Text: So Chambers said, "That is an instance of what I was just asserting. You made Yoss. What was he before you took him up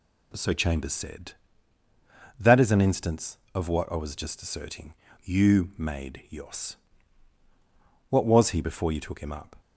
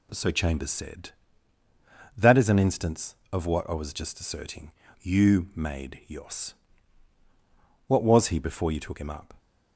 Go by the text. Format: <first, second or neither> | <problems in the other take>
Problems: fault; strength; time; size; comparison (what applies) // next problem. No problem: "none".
neither | none